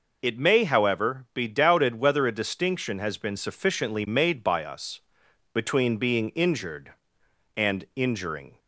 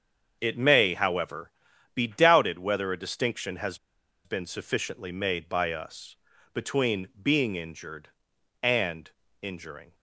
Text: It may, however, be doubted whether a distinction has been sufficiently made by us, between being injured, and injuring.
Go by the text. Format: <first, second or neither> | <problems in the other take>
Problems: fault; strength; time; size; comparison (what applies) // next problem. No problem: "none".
first | starts louder than the rest; until 1.4 s; 7 dB // pauses between "has" and "been"; noticeable; at 3.7 s; 0.48 s long // pauses between "and" and "injuring"; slight; at 9.0 s; 0.32 s long